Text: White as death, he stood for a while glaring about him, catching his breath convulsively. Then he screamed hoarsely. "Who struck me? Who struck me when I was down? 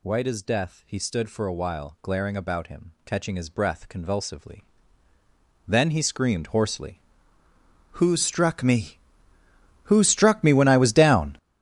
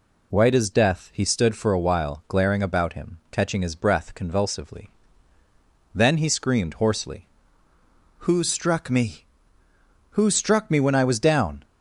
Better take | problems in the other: second | gets louder; strong; throughout; 12.5 dB

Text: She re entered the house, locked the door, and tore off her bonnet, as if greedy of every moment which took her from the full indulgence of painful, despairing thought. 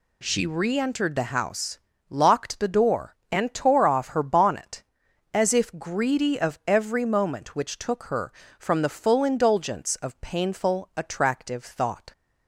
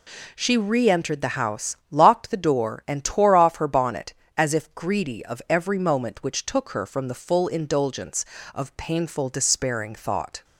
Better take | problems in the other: second | says "attractive" for "despairing"; at 10.9 s

